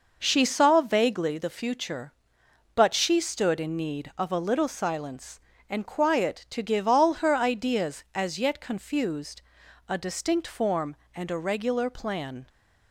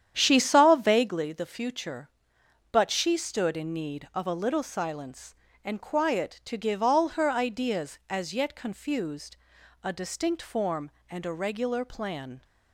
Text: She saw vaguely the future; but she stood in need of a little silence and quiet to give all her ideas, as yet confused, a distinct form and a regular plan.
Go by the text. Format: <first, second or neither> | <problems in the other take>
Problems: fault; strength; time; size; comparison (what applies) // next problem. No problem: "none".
first | starts louder than the rest; strong; until 1.1 s; 9.5 dB